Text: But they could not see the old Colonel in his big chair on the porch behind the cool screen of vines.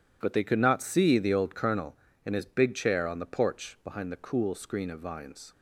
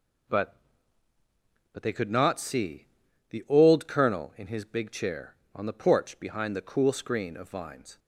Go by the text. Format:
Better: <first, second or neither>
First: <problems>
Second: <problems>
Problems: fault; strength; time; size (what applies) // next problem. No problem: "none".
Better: first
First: none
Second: says "But" twice; at 1.7 s // pauses between "see" and "the"; at 2.8 s; 0.44 s long